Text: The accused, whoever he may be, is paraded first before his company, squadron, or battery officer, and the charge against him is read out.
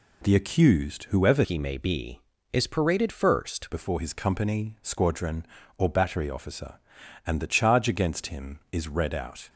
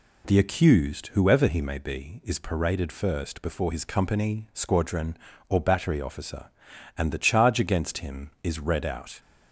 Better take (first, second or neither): second